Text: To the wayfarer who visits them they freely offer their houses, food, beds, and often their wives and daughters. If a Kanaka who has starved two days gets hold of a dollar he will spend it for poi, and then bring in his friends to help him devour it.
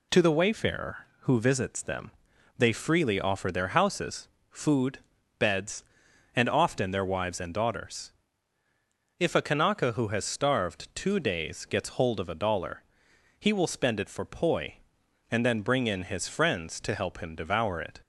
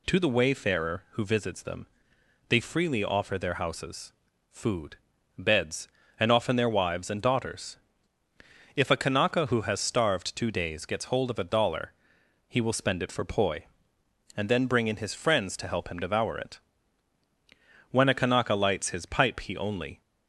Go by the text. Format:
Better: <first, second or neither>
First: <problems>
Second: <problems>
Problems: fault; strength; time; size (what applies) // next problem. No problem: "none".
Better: first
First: pauses between "them" and "they"; noticeable; at 2.0 s; 0.48 s long // pauses between "dollar" and "he"; noticeable; at 12.8 s; 0.58 s long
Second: pauses between "them" and "they"; noticeable; at 1.8 s; 0.62 s long // pauses between "dollar" and "he"; noticeable; at 11.9 s; 0.54 s long // goes on to say "When a Kanaka lights his pipe he only"; strong; from 17.8 s on; 2.1 s long